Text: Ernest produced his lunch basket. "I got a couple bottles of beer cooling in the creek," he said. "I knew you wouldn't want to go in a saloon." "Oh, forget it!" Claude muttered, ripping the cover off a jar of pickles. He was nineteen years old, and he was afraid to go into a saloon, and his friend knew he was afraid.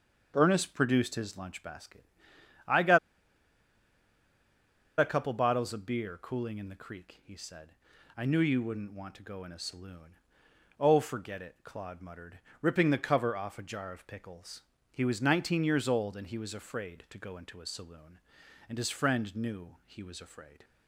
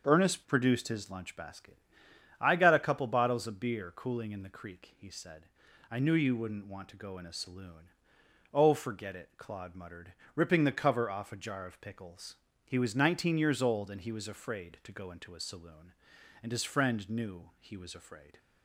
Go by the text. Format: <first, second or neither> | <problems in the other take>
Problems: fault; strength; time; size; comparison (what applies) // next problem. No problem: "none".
second | starts louder than the rest; until 1.3 s; 6.5 dB; also in the second // pauses between "got" and "a"; strong; at 2.9 s; 1.9 s long